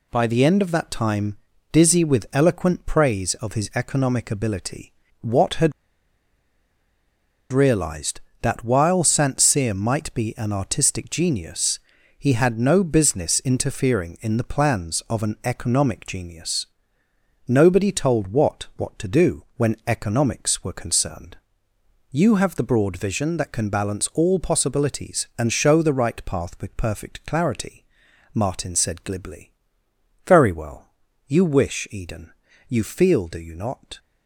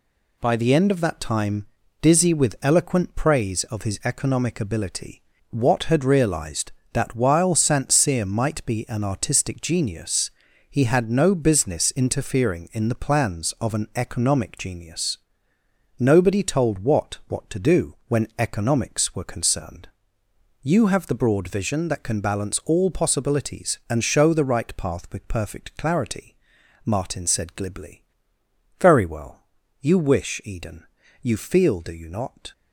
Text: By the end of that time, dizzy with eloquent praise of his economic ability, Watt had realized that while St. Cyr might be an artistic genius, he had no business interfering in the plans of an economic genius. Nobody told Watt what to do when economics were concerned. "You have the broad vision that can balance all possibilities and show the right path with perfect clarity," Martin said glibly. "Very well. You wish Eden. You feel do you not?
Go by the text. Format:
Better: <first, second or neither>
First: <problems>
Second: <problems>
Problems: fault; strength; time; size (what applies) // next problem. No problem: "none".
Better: second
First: pauses between "had" and "realized"; strong; at 5.7 s; 1.8 s long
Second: none